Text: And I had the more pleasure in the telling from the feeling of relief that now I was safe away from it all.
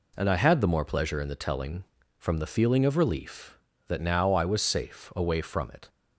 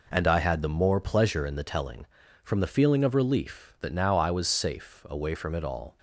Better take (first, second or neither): second